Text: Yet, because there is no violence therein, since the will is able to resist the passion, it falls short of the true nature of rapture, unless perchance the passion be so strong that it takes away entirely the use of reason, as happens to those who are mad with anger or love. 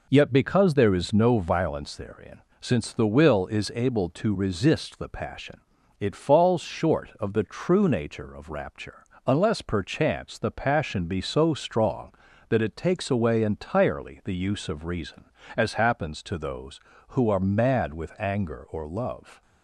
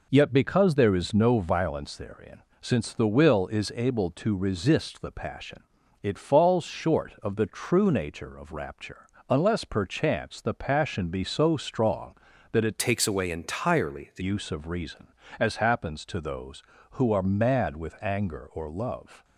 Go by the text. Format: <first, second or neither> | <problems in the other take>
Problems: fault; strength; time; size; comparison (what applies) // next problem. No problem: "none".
first | changes voice from "takes" to "the"; from 12.7 to 14.2 s; 1.5 s long